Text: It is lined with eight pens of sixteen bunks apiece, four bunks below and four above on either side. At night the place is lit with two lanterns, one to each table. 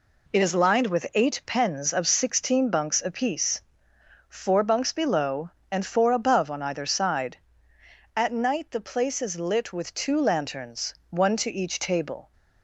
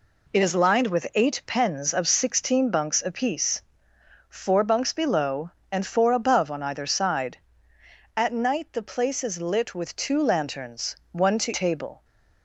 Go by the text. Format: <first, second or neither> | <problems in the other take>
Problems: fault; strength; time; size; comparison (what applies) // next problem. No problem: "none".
first | skips "each"; at 11.5 s